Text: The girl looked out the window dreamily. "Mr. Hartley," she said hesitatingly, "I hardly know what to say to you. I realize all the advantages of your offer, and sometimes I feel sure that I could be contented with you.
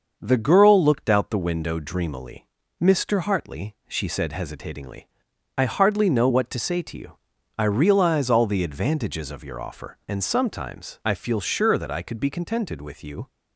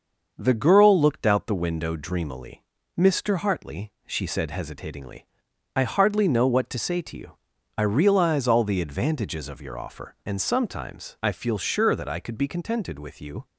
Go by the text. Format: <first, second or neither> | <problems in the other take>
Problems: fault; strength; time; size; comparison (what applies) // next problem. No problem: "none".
neither | starts louder than the rest; the same in both